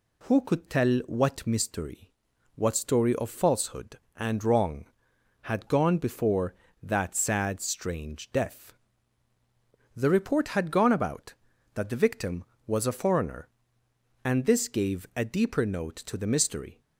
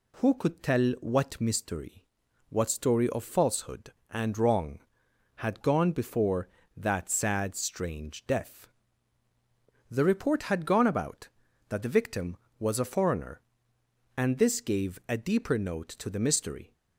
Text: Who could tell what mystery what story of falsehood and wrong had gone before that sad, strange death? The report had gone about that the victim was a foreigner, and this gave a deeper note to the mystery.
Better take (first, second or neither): neither